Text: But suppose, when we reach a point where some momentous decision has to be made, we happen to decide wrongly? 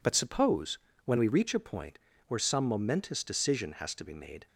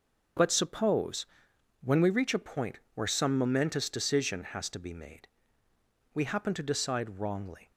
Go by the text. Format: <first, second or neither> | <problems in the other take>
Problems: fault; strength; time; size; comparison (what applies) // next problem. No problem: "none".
second | pauses between "point" and "where"; slight; at 1.9 s; 0.28 s long // stops before "we happen to decide wrongly"; at 4.4 s